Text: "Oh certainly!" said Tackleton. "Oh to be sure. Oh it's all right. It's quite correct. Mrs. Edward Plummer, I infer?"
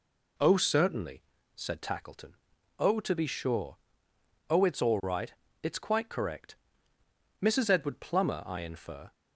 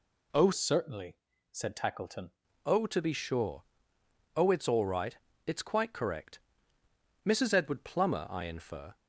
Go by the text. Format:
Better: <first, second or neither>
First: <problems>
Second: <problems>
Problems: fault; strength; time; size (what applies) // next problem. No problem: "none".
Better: first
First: none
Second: changes voice from "certainly" to "Tackleton"; from 0.5 to 2.3 s; 1.8 s long